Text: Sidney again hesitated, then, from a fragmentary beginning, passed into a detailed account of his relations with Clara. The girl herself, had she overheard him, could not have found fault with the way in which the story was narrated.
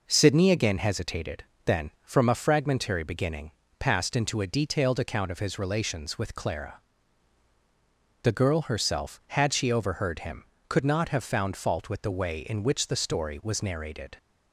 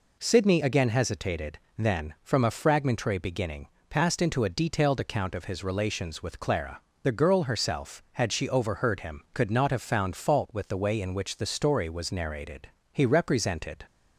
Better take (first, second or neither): first